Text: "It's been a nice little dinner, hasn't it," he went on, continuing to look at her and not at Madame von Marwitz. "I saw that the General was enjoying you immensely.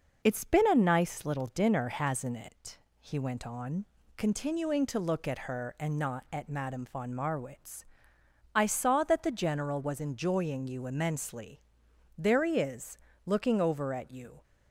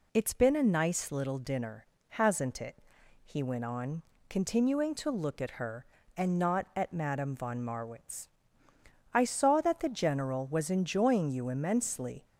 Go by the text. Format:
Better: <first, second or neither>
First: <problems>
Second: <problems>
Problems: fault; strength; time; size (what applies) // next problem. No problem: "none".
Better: second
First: goes on to say "There he is looking over at you"; strong; from 12.1 s on; 2.2 s long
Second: none